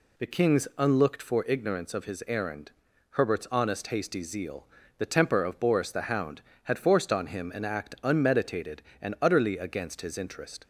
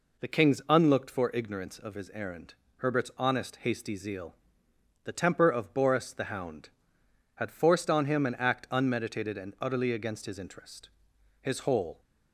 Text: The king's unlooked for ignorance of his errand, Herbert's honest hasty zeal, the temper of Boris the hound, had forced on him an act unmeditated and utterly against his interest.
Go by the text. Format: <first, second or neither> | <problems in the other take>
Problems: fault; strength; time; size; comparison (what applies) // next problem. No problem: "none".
first | goes on to say "His whole"; from 11.3 s on; 0.60 s long